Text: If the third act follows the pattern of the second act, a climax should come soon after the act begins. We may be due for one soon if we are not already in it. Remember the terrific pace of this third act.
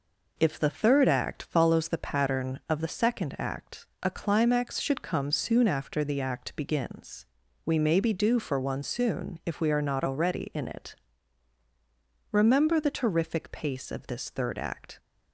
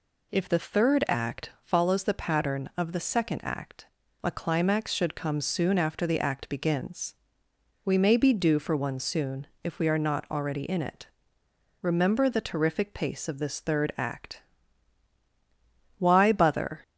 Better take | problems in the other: first | pauses between "soon" and "if"; slight; at 9.4 s; 0.18 s long // goes on to say "WHY BOTHER"; noticeable; from 15.9 s on; 0.84 s long

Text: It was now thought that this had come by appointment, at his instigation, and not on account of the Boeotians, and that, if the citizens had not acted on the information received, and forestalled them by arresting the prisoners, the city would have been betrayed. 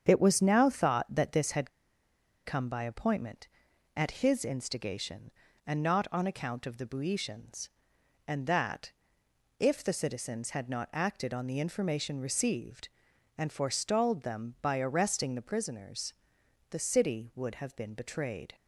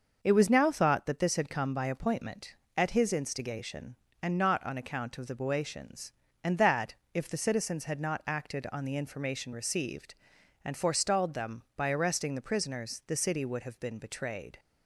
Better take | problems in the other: second | starts louder than the rest; strong; until 1.1 s; 7.5 dB; also in the second // pauses between "had" and "come"; noticeable; at 1.6 s; 0.76 s long

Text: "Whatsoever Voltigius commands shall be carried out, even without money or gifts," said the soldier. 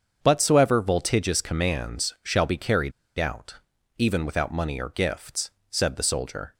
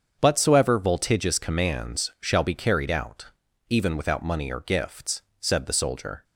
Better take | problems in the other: second | starts louder than the rest; until 1.2 s; 7 dB; also in the second // pauses between "carried" and "out"; slight; at 2.9 s; 0.25 s long

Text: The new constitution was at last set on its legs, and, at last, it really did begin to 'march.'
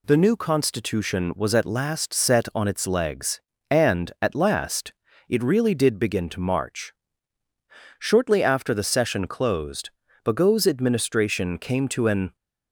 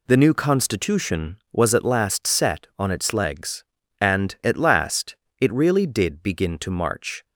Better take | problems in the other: second | goes on to say "Shortly after the session closed Bagot's administration came to an"; strong; from 7.9 s on; 4.3 s long

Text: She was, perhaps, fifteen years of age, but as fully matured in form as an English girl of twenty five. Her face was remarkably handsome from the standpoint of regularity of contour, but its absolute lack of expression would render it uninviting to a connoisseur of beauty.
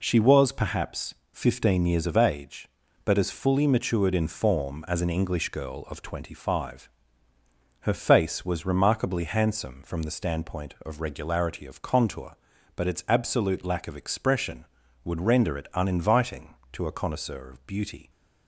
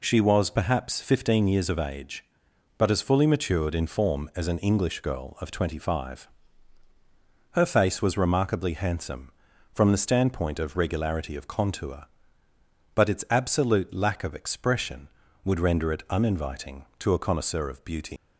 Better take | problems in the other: first | leaves "beauty" unfinished; at 18.1 s; 125 ms

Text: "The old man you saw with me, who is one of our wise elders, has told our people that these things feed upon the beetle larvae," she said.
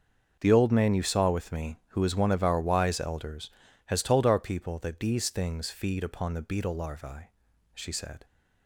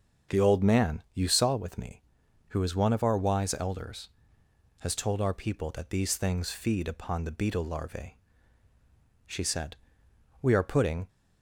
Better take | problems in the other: first | starts louder than the rest; until 1.4 s; 6.5 dB; also in the first // goes on to say "We are putting"; noticeable; from 10.3 s on; 0.68 s long

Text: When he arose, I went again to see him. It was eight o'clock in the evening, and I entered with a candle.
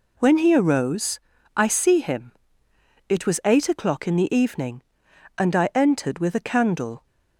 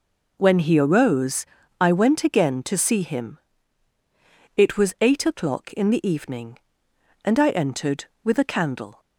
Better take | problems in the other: second | skips "went again to"; at 1.6 s

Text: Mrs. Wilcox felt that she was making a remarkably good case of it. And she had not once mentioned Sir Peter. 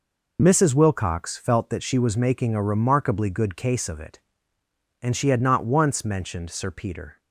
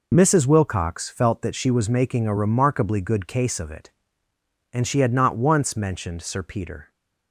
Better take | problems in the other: neither | none

